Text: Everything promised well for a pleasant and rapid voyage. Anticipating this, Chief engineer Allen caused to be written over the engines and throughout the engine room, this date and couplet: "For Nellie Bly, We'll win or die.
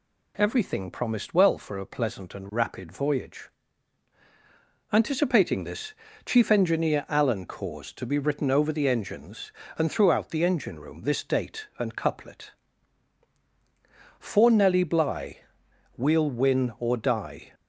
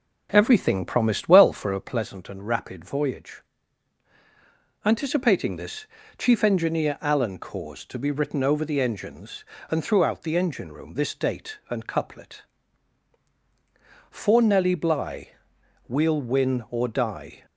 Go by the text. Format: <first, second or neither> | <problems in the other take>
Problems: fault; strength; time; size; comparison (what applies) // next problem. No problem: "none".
first | starts louder than the rest; noticeable; until 2.0 s; 4 dB